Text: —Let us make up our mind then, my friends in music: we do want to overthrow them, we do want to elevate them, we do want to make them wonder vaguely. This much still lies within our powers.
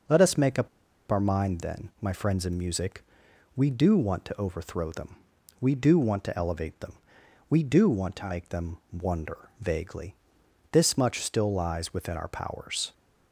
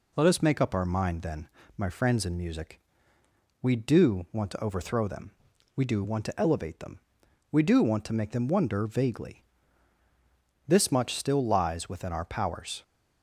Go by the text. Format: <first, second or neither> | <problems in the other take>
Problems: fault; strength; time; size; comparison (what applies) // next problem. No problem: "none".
second | pauses between "up" and "our"; at 0.6 s; 0.41 s long // pauses between "them" and "wonder"; slight; at 8.7 s; 0.16 s long